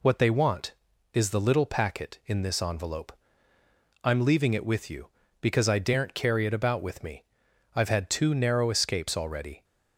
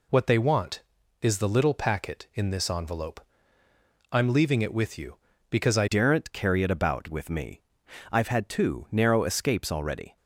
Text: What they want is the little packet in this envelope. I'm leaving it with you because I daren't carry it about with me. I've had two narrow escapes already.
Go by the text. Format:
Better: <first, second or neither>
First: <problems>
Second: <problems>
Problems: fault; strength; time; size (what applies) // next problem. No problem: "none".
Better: first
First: none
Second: changes voice at "daren't"; from 5.8 s on; 4.3 s long